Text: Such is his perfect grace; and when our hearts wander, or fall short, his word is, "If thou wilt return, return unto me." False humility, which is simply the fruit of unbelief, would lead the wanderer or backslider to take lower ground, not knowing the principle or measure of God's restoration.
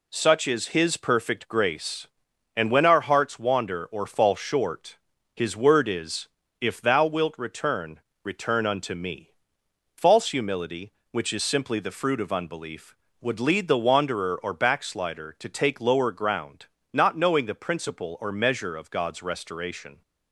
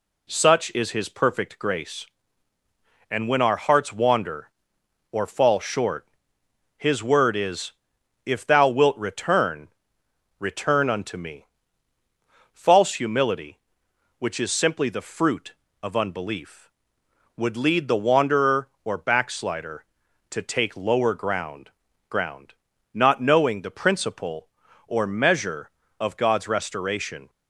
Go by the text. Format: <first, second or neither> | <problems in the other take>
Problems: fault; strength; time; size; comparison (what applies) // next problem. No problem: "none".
first | says "ground" twice; at 22.0 s